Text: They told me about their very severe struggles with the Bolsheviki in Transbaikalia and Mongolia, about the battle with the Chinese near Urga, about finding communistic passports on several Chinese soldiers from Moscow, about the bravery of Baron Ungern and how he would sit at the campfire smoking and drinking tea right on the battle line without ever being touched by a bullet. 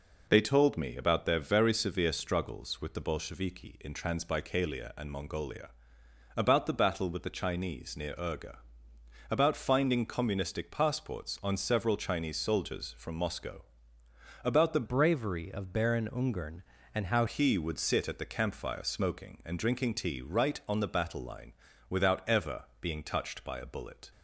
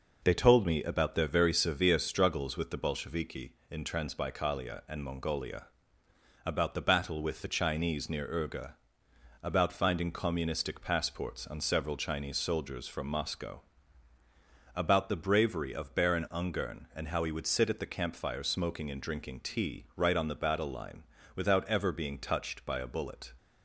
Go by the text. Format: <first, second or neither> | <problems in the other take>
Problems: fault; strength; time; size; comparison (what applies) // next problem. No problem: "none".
second | changes voice from "bravery" to "how"; from 14.8 to 17.2 s; 2.4 s long // pauses between "line" and "without"; slight; at 21.5 s; 0.36 s long; slight in the second // pauses between "ever" and "being"; slight; at 22.6 s; 0.16 s long